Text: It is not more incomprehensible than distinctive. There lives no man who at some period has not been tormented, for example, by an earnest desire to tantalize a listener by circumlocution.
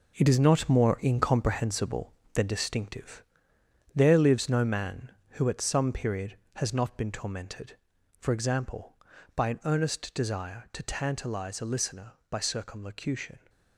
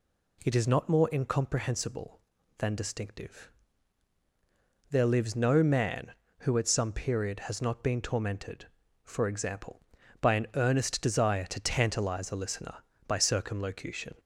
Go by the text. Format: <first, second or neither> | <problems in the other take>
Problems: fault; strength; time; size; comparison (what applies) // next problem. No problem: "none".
second | gets quieter; strong; throughout; 8.5 dB